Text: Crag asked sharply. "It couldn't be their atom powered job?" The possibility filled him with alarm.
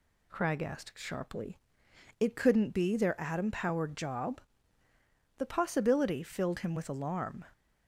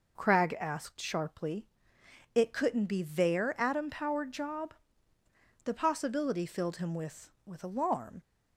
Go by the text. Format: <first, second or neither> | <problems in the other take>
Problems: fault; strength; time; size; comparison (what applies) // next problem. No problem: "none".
first | says "with" twice; at 7.4 s